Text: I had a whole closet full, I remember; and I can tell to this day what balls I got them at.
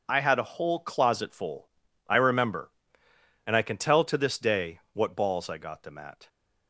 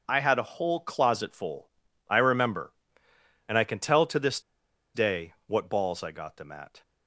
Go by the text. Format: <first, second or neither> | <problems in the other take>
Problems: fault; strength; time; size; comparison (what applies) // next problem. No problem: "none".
first | pauses between "this" and "day"; noticeable; at 4.3 s; 0.54 s long